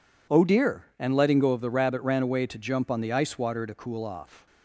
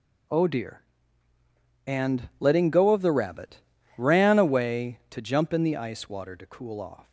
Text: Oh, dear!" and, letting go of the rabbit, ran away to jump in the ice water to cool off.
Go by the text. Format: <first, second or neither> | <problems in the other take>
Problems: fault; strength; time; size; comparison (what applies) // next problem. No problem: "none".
second | says "on" for "in"; at 2.8 s